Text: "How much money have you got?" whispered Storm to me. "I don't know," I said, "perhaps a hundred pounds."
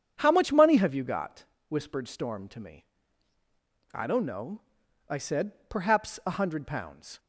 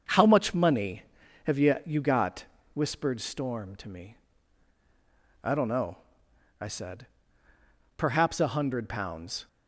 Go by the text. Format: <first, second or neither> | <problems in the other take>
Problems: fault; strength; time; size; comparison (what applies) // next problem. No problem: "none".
first | starts louder than the rest; until 1.4 s; 6.5 dB; strong in the first // says "you" twice; at 1.8 s